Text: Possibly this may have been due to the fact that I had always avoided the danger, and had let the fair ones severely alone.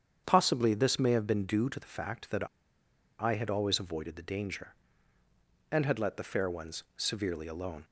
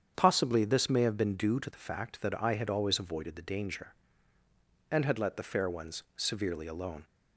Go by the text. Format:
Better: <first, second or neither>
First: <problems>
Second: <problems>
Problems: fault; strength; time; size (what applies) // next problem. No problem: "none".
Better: second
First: starts louder than the rest; strong; until 1.2 s; 8 dB // pauses between "that" and "I"; noticeable; at 2.4 s; 0.74 s long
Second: starts louder than the rest; strong; until 1.1 s; 8 dB